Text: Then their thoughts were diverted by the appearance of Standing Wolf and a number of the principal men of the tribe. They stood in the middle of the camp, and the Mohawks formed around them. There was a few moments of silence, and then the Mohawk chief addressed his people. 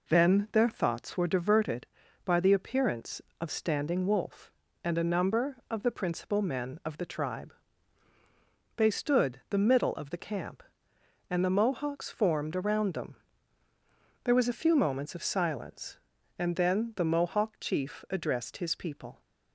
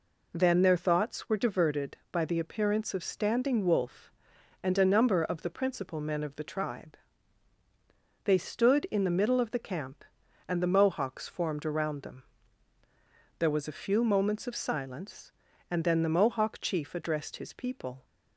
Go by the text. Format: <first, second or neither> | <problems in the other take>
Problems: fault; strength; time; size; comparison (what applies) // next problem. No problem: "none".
second | skips "in"; at 9.4 s